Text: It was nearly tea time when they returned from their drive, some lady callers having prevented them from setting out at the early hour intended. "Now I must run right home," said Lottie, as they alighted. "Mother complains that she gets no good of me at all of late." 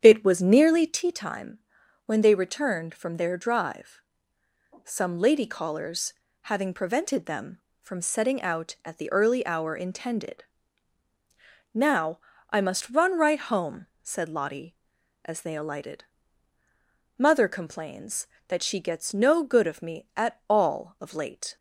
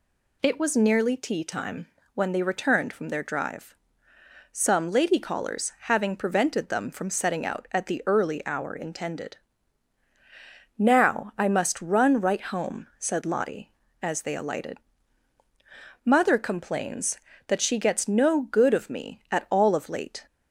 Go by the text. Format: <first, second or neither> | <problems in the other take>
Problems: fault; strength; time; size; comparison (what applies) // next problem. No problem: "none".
second | starts louder than the rest; strong; until 1.1 s; 8.5 dB // pauses between "time" and "when"; noticeable; at 1.5 s; 0.48 s long; slight in the second // pauses between "callers" and "having"; slight; at 6.1 s; 0.28 s long // pauses between "Now" and "I"; slight; at 12.1 s; 0.30 s long